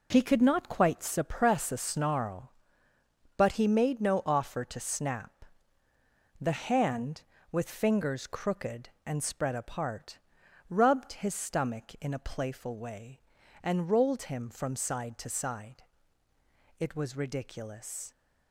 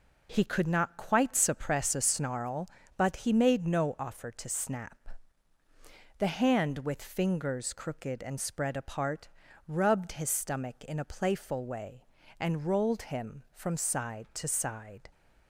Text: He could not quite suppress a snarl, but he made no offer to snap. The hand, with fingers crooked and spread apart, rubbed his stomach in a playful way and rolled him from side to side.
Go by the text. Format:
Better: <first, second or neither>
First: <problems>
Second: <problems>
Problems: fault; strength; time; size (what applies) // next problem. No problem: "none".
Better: second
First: goes on to say "It was ridiculous"; from 16.7 s on; 1.3 s long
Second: none